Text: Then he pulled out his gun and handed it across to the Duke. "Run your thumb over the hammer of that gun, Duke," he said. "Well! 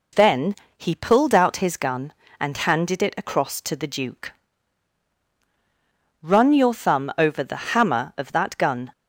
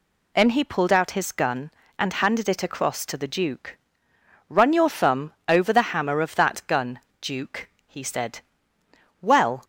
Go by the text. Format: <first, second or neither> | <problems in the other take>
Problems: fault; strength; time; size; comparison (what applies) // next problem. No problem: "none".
second | pauses between "Then" and "he"; slight; at 0.5 s; 0.24 s long // stops before "Duke he said Well"; at 8.9 s